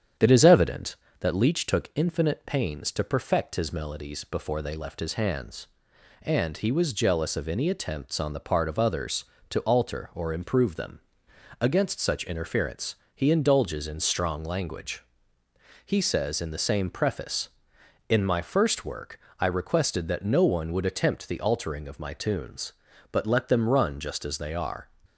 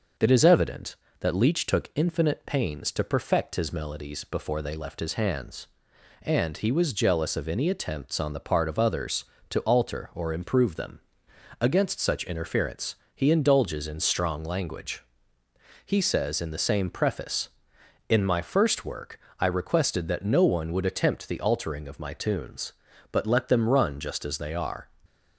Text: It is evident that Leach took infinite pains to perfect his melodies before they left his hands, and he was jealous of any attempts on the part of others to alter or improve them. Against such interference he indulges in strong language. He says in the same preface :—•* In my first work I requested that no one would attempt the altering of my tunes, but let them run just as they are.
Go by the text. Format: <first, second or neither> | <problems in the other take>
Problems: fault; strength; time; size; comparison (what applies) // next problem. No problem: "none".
second | starts louder than the rest; strong; until 1.3 s; 8.5 dB // pauses between "interference" and "he"; slight; at 12.9 s; 0.20 s long; slight in the second // pauses between "work" and "I"; slight; at 19.1 s; 0.20 s long; slight in the second